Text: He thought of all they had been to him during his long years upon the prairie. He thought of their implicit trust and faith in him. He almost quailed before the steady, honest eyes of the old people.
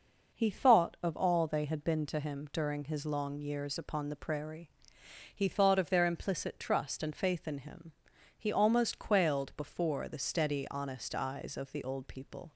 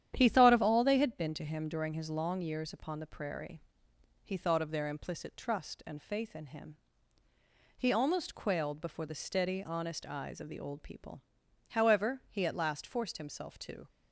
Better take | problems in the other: first | starts louder than the rest; strong; until 1.1 s; 10 dB // goes on to say "However he at last forced himself to"; strong; from 11.7 s on; 2.1 s long

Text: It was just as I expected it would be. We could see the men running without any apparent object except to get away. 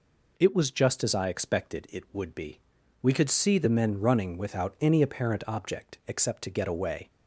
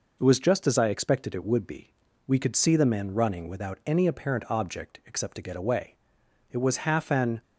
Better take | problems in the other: first | goes on to say "It was half an"; noticeable; from 6.4 s on; 0.94 s long

